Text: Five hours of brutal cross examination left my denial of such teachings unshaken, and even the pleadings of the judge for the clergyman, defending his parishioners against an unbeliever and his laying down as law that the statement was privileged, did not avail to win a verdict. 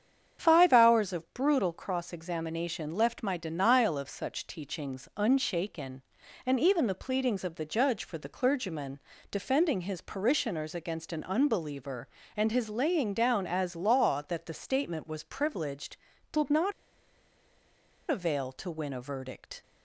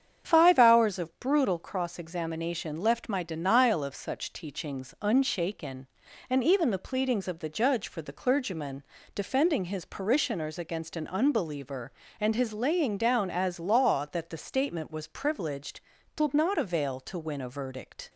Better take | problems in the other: second | starts louder than the rest; strong; until 1.4 s; 8 dB; strong in the second // pauses between "not" and "avail"; strong; at 16.7 s; 1.3 s long

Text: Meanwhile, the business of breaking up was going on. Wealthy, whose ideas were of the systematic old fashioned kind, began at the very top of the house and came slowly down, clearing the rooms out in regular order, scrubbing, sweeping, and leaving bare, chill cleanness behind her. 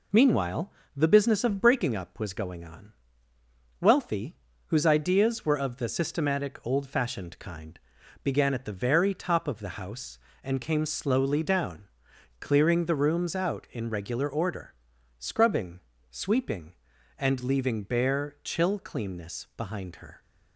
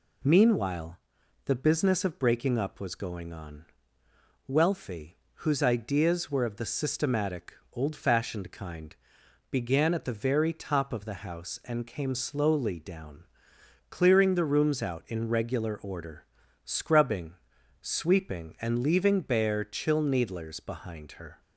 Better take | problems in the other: first | pauses between "systematic" and "old"; slight; at 7.5 s; 0.20 s long // says "needlers" for "cleanness"; at 20.0 s

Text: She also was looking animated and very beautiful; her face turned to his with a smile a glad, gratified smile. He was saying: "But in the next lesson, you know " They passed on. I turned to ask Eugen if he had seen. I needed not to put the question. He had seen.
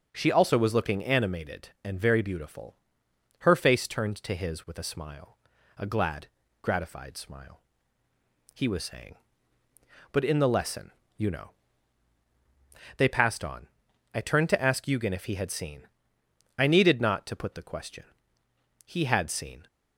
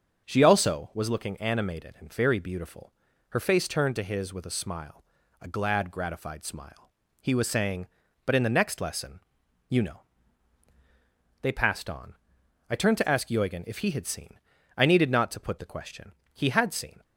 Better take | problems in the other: second | starts louder than the rest; strong; until 1.1 s; 7 dB; strong in the second // pauses between "smile" and "a"; at 5.3 s; 0.42 s long; also in the second // skips "next"; at 10.4 s

